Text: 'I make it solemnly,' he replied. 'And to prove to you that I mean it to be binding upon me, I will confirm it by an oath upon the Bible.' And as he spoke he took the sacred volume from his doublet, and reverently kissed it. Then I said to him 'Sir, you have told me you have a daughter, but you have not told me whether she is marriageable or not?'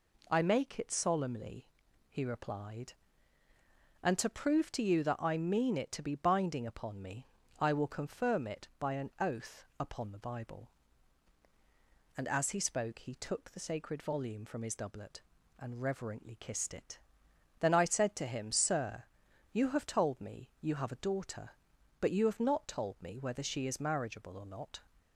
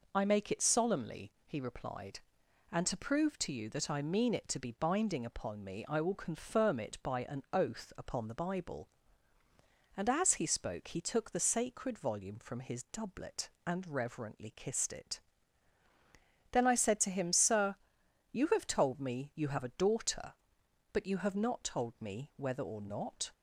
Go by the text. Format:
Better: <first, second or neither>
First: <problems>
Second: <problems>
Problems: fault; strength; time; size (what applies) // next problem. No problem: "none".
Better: first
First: none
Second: skips "she is marriageable"; at 22.6 s